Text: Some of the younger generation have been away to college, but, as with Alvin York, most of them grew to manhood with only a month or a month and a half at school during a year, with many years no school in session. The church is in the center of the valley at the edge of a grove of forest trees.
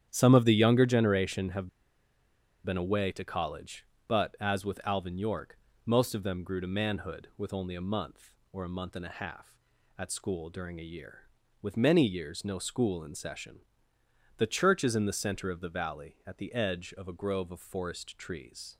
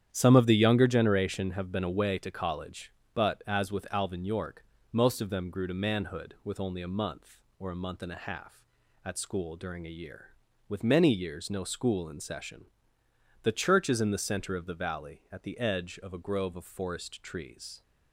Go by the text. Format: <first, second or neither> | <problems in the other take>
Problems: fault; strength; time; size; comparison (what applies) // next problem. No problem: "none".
second | starts louder than the rest; strong; until 1.1 s; 9.5 dB; strong in the second // pauses between "have" and "been"; noticeable; at 1.6 s; 0.95 s long